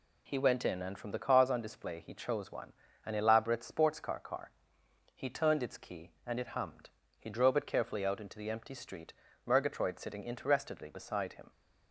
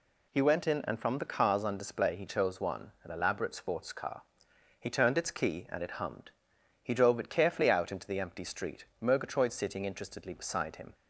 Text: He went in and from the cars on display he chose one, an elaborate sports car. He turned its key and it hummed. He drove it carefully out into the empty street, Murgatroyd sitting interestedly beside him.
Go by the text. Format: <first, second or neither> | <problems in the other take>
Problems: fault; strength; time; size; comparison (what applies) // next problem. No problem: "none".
second | says "car" twice; at 4.1 s